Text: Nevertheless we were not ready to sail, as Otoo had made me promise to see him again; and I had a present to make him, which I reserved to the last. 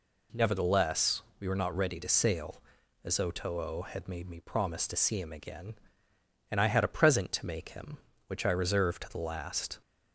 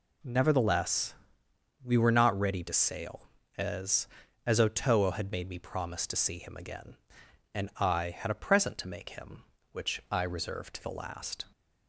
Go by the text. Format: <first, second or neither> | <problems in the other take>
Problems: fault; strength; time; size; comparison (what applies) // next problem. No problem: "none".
first | pauses between "Nevertheless" and "we"; noticeable; at 1.1 s; 0.68 s long; slight in the first // says "as" twice; at 4.4 s